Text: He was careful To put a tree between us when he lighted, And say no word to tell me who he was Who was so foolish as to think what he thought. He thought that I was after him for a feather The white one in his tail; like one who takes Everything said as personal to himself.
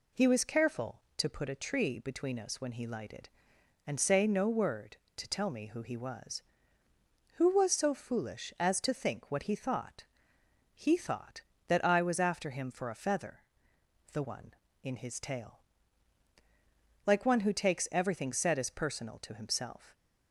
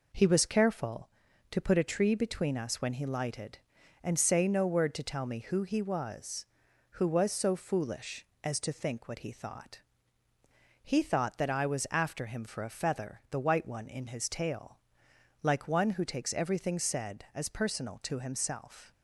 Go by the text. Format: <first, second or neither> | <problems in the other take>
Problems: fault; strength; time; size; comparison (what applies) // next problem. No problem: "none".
second | pauses between "feather" and "The"; noticeable; at 13.4 s; 0.72 s long // skips "white"; at 14.2 s